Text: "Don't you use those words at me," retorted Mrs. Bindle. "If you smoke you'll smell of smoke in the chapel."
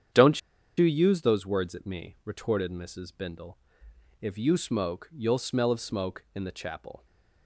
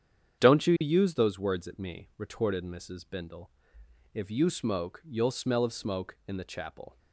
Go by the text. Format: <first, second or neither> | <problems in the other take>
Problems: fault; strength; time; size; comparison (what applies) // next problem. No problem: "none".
second | starts louder than the rest; strong; until 1.5 s; 8.5 dB; strong in the second // pauses between "Don't" and "you"; at 0.3 s; 0.39 s long